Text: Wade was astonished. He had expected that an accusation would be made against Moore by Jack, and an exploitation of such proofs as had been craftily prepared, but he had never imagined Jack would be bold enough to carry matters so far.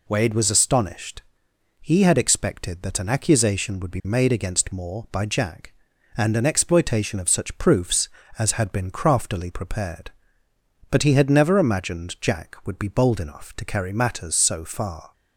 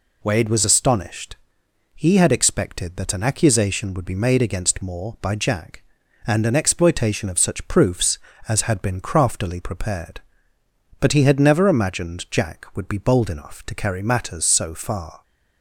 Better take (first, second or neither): neither